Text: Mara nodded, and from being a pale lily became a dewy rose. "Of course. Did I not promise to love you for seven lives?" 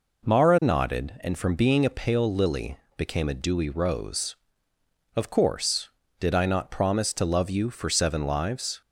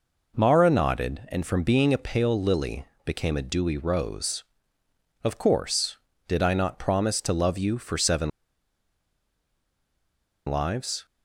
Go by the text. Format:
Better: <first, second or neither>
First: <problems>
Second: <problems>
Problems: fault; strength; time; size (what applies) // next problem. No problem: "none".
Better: first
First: pauses between "lily" and "became"; slight; at 2.7 s; 0.20 s long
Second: pauses between "lily" and "became"; slight; at 2.8 s; 0.20 s long // pauses between "seven" and "lives"; strong; at 8.3 s; 2.1 s long